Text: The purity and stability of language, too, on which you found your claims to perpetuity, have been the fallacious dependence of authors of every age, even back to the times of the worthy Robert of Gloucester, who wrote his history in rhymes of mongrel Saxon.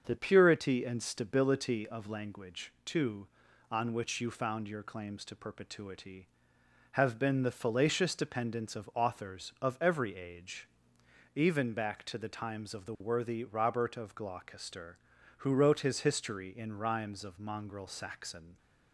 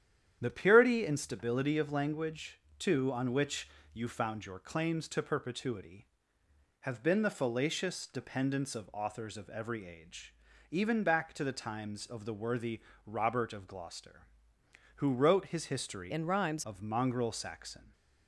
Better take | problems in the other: first | starts louder than the rest; strong; until 1.4 s; 9.5 dB; also in the first // pauses between "which" and "you"; slight; at 3.6 s; 0.26 s long // pauses between "worthy" and "Robert"; slight; at 12.7 s; 0.26 s long // changes voice from "in" to "rhymes"; from 16.1 to 16.6 s; 0.5 s long

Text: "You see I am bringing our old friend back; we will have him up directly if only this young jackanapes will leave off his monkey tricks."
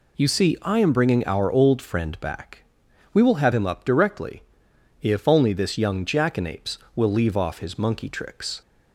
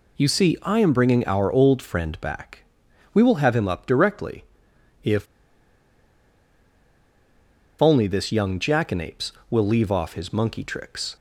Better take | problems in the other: first | pauses between "directly" and "if"; noticeable; at 4.4 s; 0.58 s long; noticeable in the first // pauses between "if" and "only"; strong; at 5.2 s; 2.5 s long

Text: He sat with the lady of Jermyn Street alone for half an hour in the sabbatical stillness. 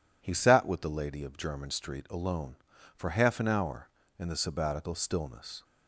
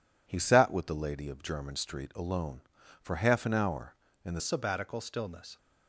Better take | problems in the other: first | changes voice at "sabbatical"; from 4.3 s on; 1.2 s long

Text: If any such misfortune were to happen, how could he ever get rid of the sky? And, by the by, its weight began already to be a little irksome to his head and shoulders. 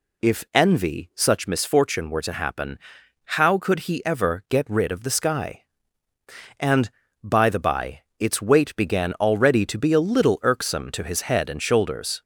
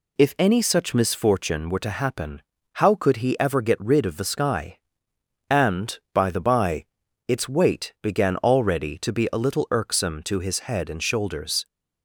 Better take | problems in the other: second | says "envy" for "any"; at 0.5 s

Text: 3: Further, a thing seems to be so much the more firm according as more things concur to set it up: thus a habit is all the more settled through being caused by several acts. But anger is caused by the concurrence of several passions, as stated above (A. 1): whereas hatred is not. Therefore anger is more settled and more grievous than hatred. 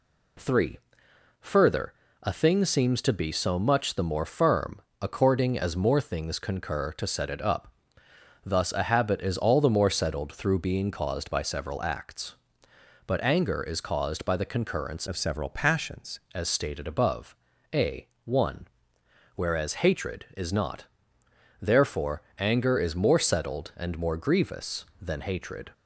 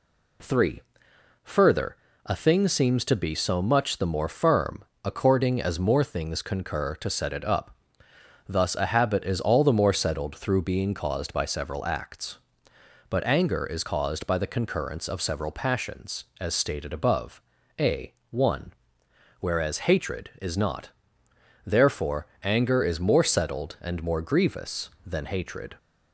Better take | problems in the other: second | pauses between "firm" and "according"; slight; at 4.7 s; 0.22 s long; slight in the second // changes voice from "of" to "passions"; from 15.0 to 16.1 s; 1.1 s long // pauses between "Therefore" and "anger"; slight; at 22.2 s; 0.18 s long; slight in the second

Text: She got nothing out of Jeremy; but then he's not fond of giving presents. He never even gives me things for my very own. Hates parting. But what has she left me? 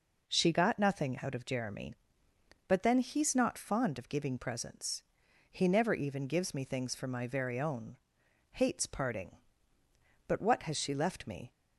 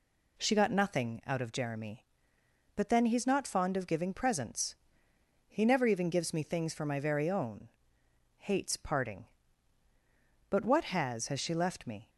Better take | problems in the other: first | says "has" twice; at 11.2 s

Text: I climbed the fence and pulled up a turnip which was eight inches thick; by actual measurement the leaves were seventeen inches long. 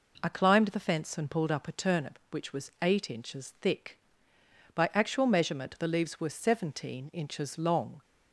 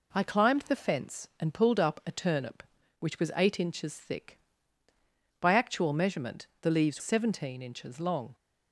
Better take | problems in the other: first | skips "were"; at 7.0 s

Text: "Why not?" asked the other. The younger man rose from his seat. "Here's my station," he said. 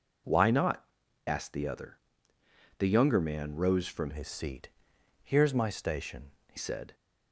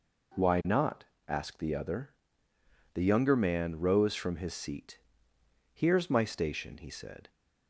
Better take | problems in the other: second | changes voice from "his" to "he"; from 4.1 to 6.5 s; 2.4 s long

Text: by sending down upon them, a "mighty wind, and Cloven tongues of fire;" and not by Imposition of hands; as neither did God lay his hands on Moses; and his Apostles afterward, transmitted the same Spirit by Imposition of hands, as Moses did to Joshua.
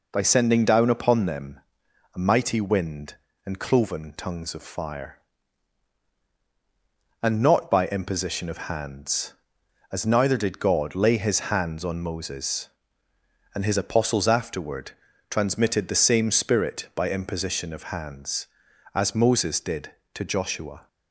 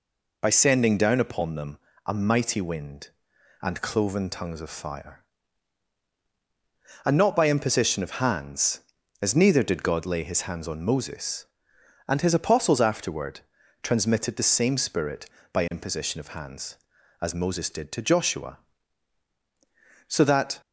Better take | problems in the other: first | goes on to say "So that"; from 20.0 s on; 0.52 s long

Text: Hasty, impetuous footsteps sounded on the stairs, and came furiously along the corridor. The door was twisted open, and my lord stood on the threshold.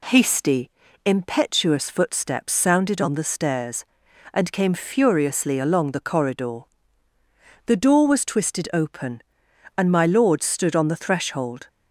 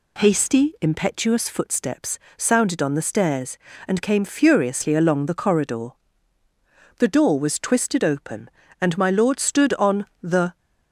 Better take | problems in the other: first | pauses between "footsteps" and "sounded"; slight; at 2.1 s; 0.22 s long // pauses between "on" and "the"; slight; at 10.0 s; 0.16 s long // stops before "threshold"; at 10.5 s

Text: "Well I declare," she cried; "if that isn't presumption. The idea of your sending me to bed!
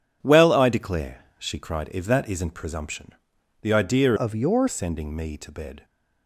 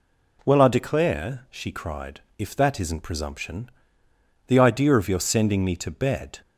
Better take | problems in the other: second | changes voice from "of" to "your"; from 4.1 to 4.6 s; 0.5 s long

